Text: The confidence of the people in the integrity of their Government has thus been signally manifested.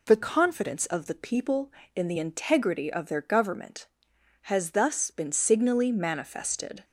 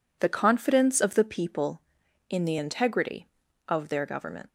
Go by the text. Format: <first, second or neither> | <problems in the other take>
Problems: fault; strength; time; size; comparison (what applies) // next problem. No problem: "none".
first | stops before "has thus been signally manifested"; at 4.4 s